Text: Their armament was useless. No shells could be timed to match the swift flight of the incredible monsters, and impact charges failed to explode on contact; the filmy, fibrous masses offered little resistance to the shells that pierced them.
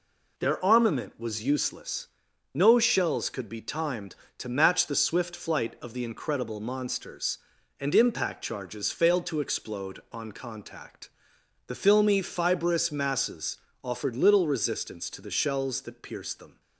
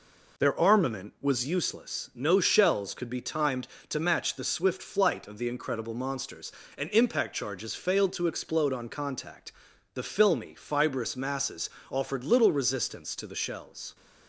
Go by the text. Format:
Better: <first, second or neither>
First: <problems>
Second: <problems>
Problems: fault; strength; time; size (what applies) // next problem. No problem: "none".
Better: first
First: pauses between "masses" and "offered"; slight; at 13.5 s; 0.26 s long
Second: pauses between "masses" and "offered"; slight; at 11.7 s; 0.18 s long // stops before "that pierced them"; at 13.9 s